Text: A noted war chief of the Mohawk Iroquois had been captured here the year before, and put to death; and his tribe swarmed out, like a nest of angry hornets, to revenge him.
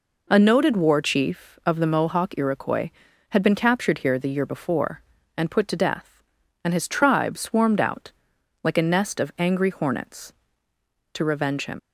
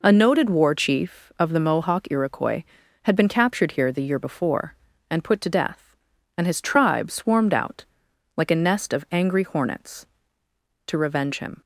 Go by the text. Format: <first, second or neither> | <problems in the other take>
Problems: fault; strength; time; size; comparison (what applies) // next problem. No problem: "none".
second | leaves "him" unfinished; at 11.7 s; 80 ms